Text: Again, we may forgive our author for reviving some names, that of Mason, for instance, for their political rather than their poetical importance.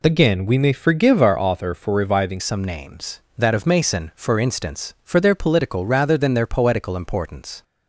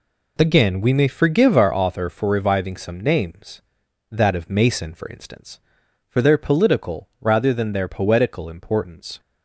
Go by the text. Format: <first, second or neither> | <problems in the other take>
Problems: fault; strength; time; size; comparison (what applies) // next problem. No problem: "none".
second | changes voice at "some"; from 2.3 s on; 5.3 s long